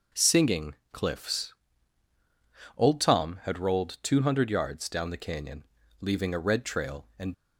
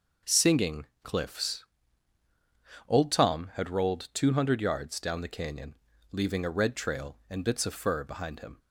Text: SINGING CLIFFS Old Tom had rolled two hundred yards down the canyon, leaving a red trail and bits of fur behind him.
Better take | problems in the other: second | starts louder than the rest; until 1.3 s; 6 dB; noticeable in the second // pauses between "SINGING" and "CLIFFS"; slight; at 0.7 s; 0.18 s long; slight in the second // pauses between "CLIFFS" and "Old"; at 1.5 s; 1.2 s long; also in the second // stops before "bits of fur behind him"; at 7.3 s

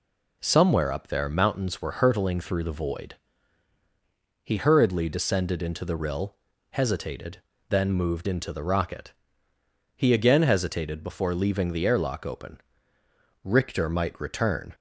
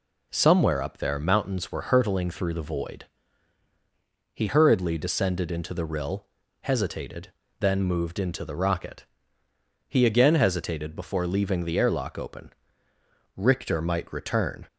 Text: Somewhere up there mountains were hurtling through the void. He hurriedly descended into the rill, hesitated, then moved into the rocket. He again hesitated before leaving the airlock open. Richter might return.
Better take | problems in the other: neither | none

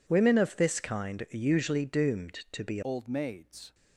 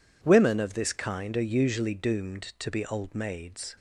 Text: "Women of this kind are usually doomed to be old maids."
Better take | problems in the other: second | changes voice at "old"; from 2.8 s on; 0.9 s long

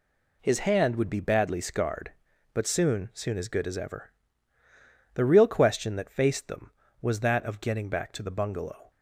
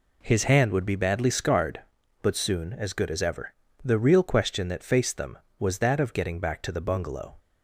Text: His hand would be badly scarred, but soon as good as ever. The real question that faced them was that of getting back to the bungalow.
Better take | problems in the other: second | says "soon" twice; at 3.1 s

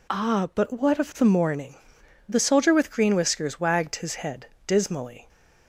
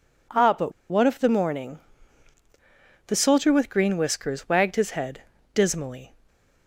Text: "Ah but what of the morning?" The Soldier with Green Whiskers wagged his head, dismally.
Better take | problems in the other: first | pauses between "but" and "what"; slight; at 0.7 s; 0.18 s long

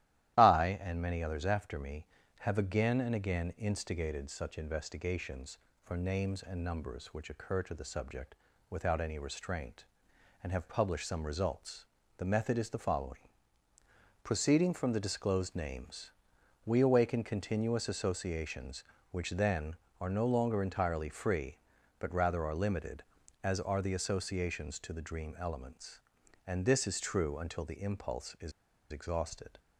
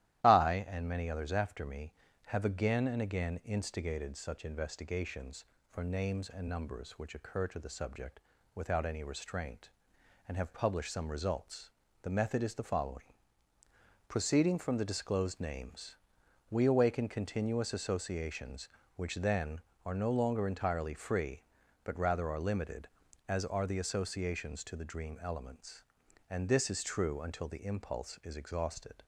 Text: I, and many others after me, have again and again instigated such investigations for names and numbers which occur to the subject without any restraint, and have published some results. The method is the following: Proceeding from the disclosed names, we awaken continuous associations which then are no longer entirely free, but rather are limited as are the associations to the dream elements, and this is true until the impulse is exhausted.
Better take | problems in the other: second | starts louder than the rest; strong; until 1.4 s; 13.5 dB; strong in the second // pauses between "subject" and "without"; slight; at 8.3 s; 0.36 s long; slight in the second // pauses between "is" and "exhausted"; at 28.5 s; 0.40 s long

